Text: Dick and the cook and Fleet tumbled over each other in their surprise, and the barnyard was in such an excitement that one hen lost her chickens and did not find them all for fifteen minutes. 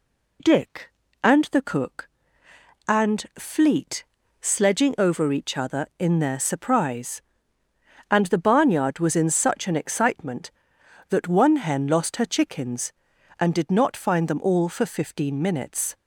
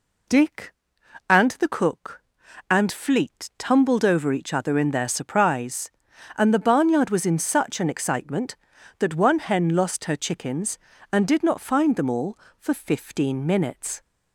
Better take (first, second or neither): second